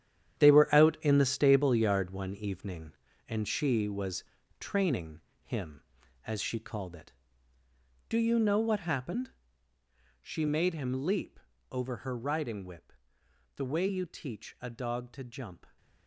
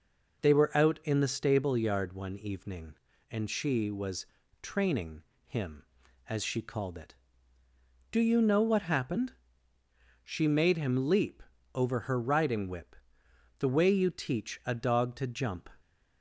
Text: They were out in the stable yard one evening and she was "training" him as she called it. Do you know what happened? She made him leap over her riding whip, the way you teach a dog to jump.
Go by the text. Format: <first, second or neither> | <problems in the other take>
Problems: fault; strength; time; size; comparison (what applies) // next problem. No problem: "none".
second | gets quieter; strong; throughout; 11 dB // pauses between "was" and "training"; at 4.2 s; 0.38 s long; also in the second // pauses between "training" and "him"; slight; at 5.1 s; 0.22 s long; slight in the second // pauses between "leap" and "over"; slight; at 11.3 s; 0.32 s long; slight in the second